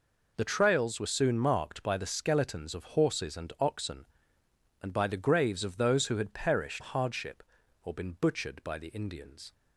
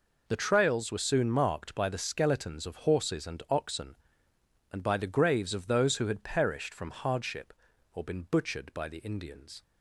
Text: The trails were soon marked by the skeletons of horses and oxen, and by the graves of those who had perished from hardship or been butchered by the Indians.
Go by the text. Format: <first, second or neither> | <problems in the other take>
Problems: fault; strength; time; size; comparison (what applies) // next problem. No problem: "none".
second | skips "from"; at 6.8 s